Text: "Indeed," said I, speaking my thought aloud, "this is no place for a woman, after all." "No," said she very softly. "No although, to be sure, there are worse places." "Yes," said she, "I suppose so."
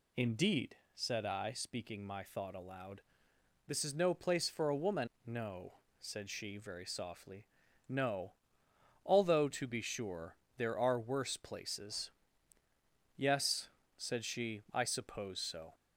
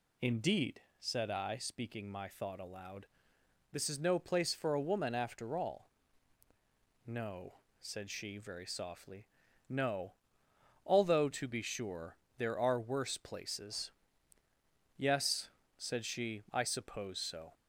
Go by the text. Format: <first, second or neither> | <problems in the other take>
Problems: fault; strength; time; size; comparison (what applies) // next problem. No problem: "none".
second | skips "after all"; at 5.1 s // pauses between "No" and "although"; noticeable; at 8.3 s; 0.70 s long; noticeable in the second